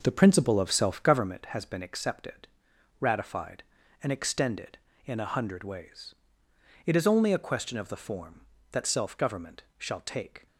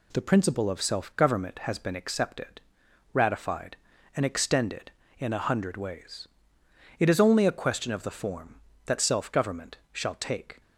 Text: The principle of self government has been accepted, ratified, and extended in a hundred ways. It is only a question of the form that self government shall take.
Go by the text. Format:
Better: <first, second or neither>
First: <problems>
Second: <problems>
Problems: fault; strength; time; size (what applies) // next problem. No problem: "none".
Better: second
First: starts louder than the rest; noticeable; until 1.3 s; 5.5 dB // pauses between "government" and "shall"; slight; at 9.6 s; 0.16 s long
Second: pauses between "government" and "shall"; slight; at 9.7 s; 0.16 s long